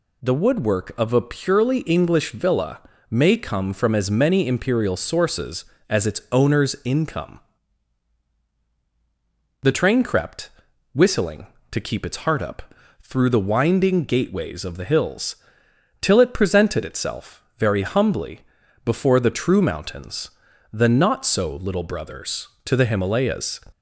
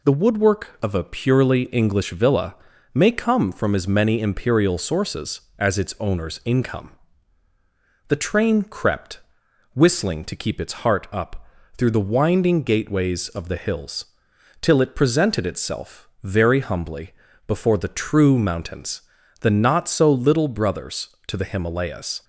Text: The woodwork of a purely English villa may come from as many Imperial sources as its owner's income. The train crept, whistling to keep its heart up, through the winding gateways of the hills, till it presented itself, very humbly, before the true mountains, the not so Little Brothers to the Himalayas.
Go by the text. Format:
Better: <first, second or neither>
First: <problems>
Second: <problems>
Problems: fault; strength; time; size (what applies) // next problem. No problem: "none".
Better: neither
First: pauses between "villa" and "may"; slight; at 2.7 s; 0.30 s long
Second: pauses between "villa" and "may"; at 2.5 s; 0.38 s long